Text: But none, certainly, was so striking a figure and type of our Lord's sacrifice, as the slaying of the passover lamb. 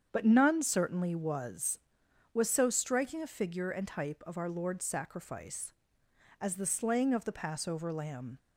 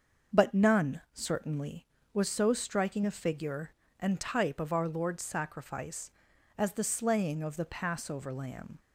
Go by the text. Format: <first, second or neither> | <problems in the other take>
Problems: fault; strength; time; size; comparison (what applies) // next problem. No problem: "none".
second | starts louder than the rest; strong; until 1.1 s; 7.5 dB; also in the second // says "was" twice; at 2.3 s